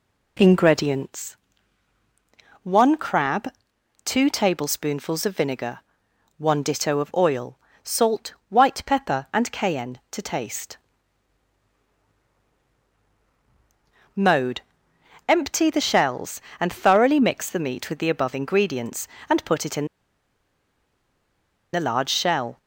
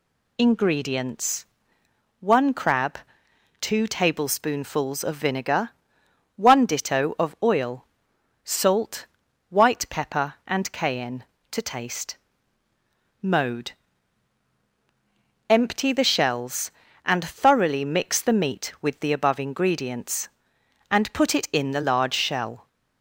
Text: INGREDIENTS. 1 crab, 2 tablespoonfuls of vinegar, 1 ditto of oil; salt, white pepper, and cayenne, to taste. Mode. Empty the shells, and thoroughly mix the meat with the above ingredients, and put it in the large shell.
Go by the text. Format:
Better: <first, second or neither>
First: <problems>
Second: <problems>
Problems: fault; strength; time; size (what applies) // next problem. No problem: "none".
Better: second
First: pauses between "in" and "the"; strong; at 19.8 s; 1.8 s long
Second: none